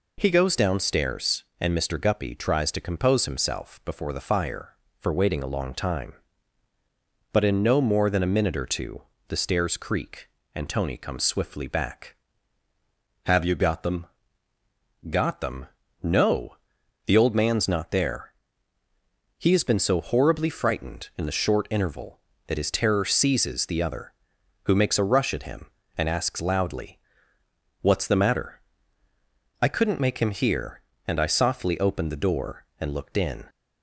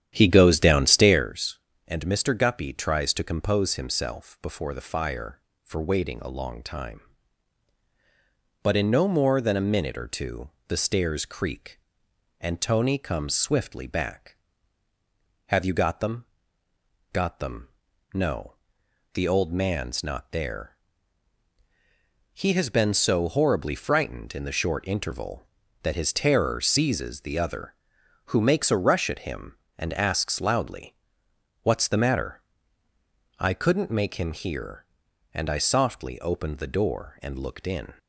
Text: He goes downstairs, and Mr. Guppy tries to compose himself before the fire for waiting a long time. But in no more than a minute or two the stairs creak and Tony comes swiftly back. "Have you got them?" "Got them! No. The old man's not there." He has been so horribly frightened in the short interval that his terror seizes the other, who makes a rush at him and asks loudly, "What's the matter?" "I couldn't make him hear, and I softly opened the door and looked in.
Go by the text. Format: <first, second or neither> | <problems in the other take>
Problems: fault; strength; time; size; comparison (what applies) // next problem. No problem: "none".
first | starts louder than the rest; strong; until 1.3 s; 10 dB // pauses between "two" and "the"; slight; at 10.4 s; 0.18 s long; slight in the first